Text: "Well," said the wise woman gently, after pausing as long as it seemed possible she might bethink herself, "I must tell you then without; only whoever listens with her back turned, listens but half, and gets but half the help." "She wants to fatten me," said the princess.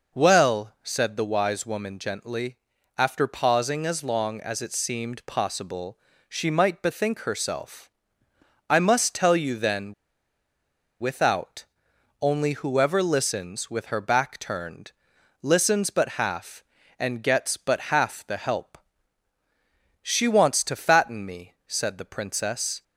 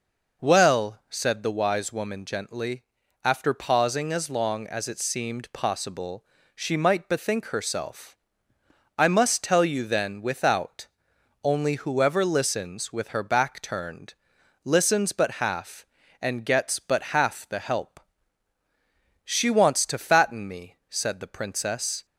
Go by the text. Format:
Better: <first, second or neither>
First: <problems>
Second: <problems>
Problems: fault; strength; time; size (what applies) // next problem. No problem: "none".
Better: second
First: pauses between "possible" and "she"; slight; at 5.9 s; 0.32 s long // pauses between "then" and "without"; at 9.9 s; 1.0 s long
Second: pauses between "possible" and "she"; slight; at 6.2 s; 0.32 s long